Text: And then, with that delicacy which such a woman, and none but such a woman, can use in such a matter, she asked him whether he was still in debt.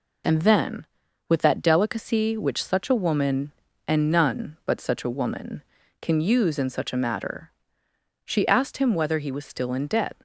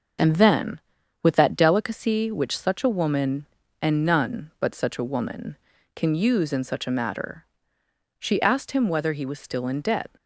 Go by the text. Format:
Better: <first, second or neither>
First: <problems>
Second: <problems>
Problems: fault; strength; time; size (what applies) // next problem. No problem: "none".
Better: first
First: none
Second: starts louder than the rest; until 1.9 s; 6.5 dB